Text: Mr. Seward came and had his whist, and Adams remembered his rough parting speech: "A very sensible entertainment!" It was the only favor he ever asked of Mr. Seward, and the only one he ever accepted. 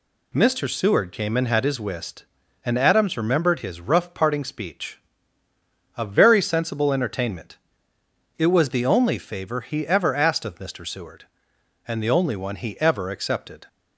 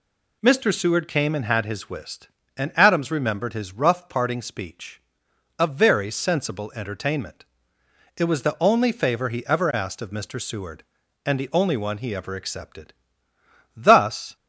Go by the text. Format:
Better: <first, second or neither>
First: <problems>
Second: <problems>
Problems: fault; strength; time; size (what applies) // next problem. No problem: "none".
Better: first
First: none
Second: goes on to say "Thus"; from 13.7 s on; 0.60 s long